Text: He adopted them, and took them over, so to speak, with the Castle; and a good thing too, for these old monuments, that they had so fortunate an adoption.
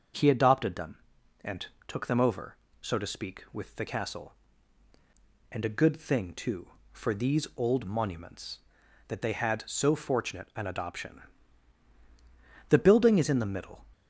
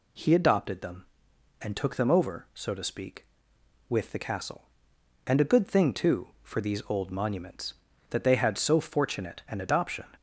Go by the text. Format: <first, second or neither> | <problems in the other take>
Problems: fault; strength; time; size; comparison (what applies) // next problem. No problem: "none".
second | starts louder than the rest; until 1.5 s; 6.5 dB // pauses between "and" and "took"; slight; at 1.6 s; 0.22 s long // goes on to say "The building is in the middle"; noticeable; from 12.6 s on; 1.1 s long